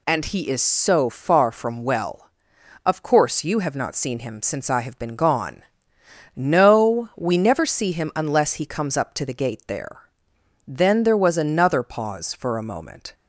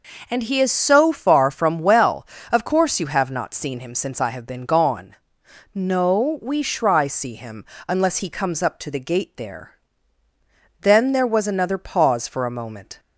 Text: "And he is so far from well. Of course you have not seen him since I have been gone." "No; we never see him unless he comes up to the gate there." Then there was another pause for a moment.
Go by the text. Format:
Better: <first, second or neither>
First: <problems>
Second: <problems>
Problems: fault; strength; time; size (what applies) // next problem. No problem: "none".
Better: first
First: none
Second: says "shry" for "never"; at 6.6 s // pauses between "him" and "unless"; slight; at 7.6 s; 0.22 s long